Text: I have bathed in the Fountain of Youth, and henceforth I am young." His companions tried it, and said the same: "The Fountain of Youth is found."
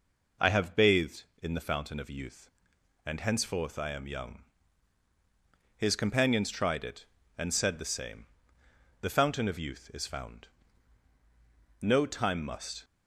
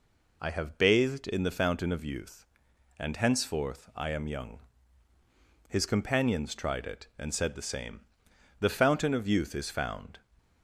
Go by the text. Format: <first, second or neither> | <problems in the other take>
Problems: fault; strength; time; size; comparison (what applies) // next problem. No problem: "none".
second | goes on to say "No time must"; noticeable; from 11.8 s on; 1.0 s long